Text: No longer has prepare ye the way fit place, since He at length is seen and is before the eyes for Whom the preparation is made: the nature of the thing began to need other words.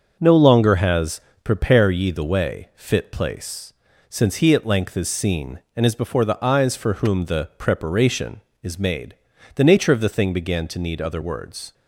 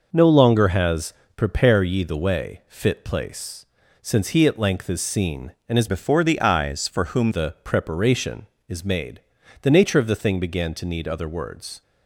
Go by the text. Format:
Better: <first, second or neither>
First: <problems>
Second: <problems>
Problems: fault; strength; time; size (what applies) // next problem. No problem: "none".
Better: first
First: pauses between "has" and "prepare"; slight; at 1.1 s; 0.24 s long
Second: pauses between "has" and "prepare"; slight; at 1.1 s; 0.24 s long // changes voice from "before" to "Whom"; from 5.8 to 7.2 s; 1.4 s long